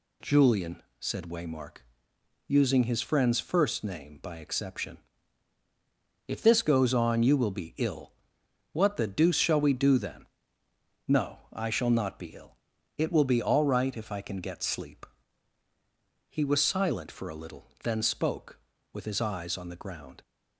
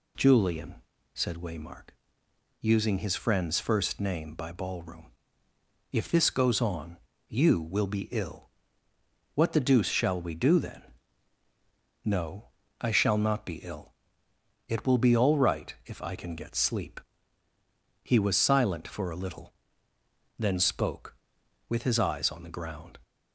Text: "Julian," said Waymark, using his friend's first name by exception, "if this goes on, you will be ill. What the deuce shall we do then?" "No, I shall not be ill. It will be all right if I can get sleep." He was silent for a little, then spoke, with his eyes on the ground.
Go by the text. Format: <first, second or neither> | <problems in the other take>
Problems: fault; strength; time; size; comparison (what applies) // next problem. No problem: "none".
first | says "ballroom" for "exception"; at 4.4 s